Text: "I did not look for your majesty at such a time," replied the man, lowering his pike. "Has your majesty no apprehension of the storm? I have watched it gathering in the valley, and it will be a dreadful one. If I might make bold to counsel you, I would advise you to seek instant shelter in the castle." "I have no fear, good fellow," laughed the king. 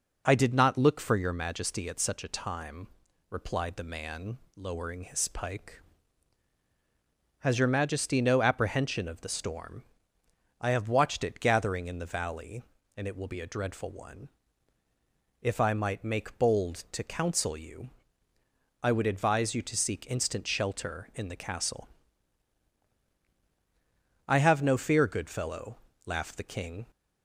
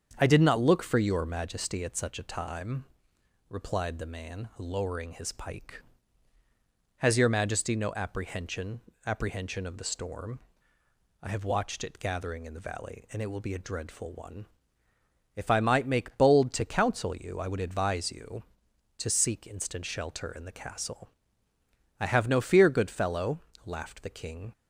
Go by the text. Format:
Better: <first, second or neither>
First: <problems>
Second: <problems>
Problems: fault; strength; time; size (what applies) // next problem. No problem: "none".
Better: first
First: none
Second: starts louder than the rest; strong; until 1.1 s; 7.5 dB // says "apprehension" twice; at 9.0 s